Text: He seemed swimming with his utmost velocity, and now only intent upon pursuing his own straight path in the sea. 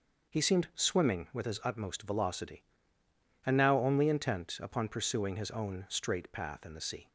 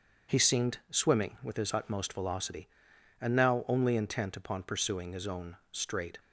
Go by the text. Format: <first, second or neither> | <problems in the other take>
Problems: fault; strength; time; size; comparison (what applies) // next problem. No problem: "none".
first | starts louder than the rest; until 1.4 s; 6.5 dB // pauses between "own" and "straight"; slight; at 5.5 s; 0.16 s long // stops before "path in the sea"; at 6.1 s